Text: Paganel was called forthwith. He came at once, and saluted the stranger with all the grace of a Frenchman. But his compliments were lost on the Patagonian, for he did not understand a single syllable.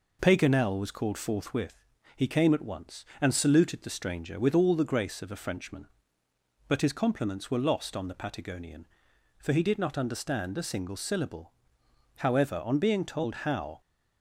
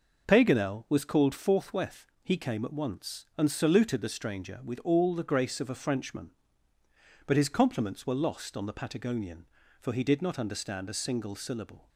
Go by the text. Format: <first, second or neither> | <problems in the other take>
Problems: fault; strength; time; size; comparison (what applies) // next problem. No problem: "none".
second | goes on to say "However on being told how"; from 12.1 s on; 1.6 s long